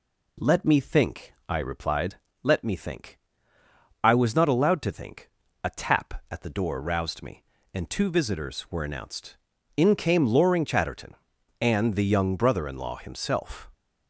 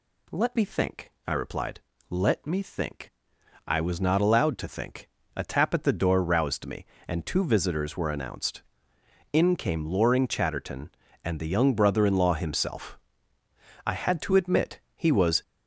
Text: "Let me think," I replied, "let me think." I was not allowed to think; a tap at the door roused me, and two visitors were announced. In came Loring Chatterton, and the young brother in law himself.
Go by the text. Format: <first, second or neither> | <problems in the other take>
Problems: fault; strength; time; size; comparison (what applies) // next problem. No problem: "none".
first | goes on to say "I had to admit he was"; from 13.8 s on; 1.5 s long